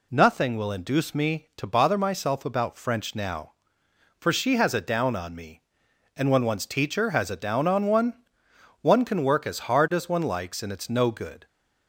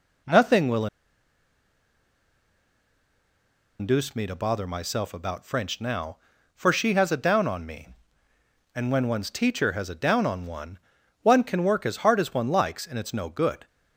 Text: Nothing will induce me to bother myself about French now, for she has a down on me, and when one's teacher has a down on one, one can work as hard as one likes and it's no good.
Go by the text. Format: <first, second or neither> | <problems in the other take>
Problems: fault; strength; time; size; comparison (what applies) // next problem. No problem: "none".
first | pauses between "will" and "induce"; strong; at 0.8 s; 2.9 s long